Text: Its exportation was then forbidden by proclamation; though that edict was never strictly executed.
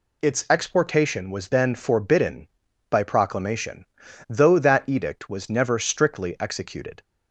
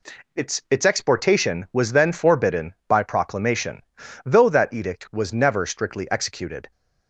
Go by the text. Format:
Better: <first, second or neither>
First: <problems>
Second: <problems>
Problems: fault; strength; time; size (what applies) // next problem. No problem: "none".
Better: first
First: none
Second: says "Its" twice; at 0.7 s